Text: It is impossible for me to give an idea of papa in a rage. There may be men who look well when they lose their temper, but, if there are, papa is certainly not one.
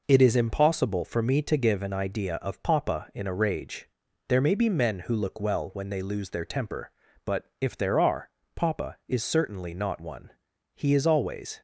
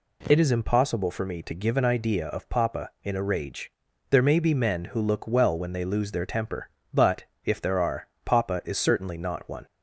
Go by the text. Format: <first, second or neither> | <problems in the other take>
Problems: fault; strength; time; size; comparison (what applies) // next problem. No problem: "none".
second | goes on to say "He is always"; noticeable; from 10.7 s on; 0.86 s long